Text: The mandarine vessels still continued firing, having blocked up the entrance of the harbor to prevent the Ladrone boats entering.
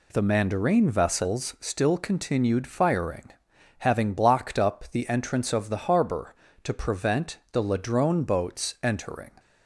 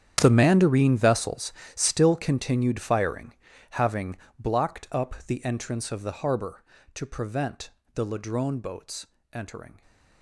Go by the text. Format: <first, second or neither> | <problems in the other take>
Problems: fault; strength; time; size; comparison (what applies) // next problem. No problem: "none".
first | gets quieter; strong; throughout; 16.5 dB // pauses between "vessels" and "still"; slight; at 1.5 s; 0.22 s long // pauses between "having" and "blocked"; slight; at 4.1 s; 0.20 s long // pauses between "prevent" and "the"; slight; at 7.6 s; 0.24 s long // pauses between "boats" and "entering"; slight; at 9.0 s; 0.24 s long